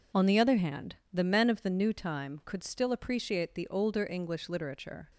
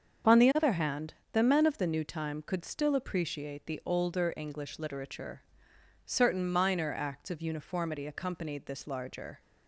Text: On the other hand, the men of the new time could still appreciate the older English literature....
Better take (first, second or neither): first